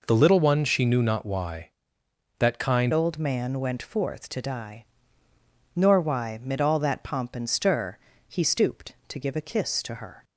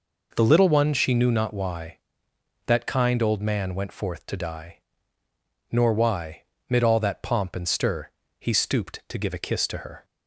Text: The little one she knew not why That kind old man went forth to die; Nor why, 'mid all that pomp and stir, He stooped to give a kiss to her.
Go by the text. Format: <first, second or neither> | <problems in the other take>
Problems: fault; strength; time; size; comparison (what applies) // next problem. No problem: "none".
second | changes voice at "old"; from 2.9 s on; 7.3 s long